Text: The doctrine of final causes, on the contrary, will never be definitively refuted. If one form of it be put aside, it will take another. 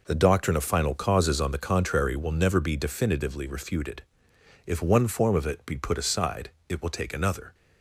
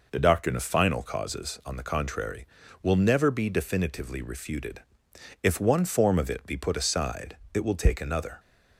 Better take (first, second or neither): neither